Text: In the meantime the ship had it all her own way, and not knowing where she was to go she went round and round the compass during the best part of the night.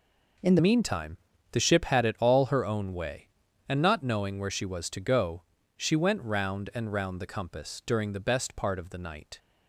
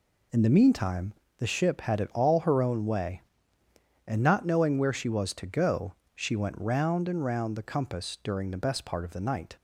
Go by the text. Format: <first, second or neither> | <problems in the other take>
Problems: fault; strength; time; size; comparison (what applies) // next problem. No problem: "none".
second | changes voice at "meantime"; from 0.5 s on; 8.8 s long // pauses between "meantime" and "the"; slight; at 1.1 s; 0.34 s long; slight in the second // pauses between "go" and "she"; slight; at 5.4 s; 0.34 s long; slight in the second